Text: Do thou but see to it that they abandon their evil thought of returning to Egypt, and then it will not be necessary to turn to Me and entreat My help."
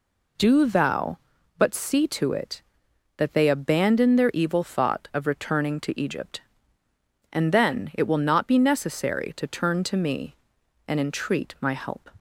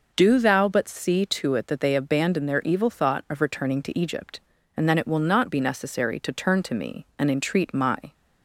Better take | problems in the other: first | stops before "help"; at 8.1 s

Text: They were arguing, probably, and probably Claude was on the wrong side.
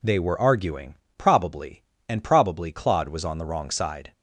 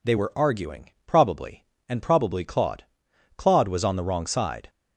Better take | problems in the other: first | says "Claude" twice; at 3.3 s

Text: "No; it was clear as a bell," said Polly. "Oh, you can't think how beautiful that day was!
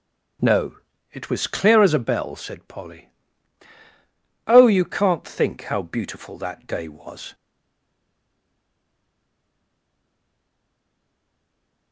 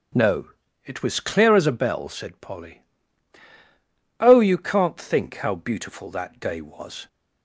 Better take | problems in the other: second | starts louder than the rest; strong; until 1.7 s; 9 dB; strong in the second // stays silent after the last word; strong; from 7.3 s on; 4.6 s long

